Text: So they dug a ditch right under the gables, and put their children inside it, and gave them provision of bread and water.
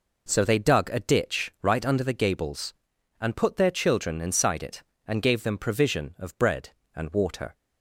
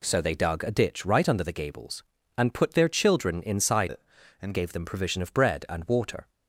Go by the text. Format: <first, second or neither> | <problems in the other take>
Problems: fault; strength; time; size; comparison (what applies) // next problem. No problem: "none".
first | changes voice from "it" to "and"; from 3.8 to 4.5 s; 0.7 s long